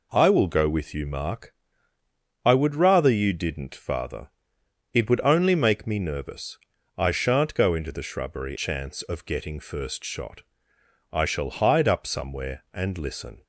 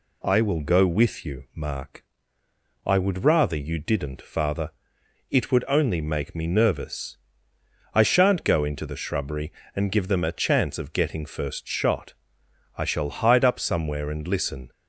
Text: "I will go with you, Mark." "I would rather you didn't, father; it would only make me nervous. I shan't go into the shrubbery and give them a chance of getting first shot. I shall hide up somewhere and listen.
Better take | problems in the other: second | skips "and give them a"; at 8.5 s

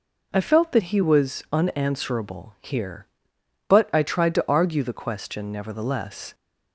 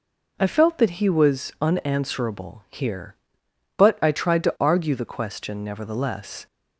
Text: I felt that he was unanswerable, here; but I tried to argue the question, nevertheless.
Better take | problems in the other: neither | none

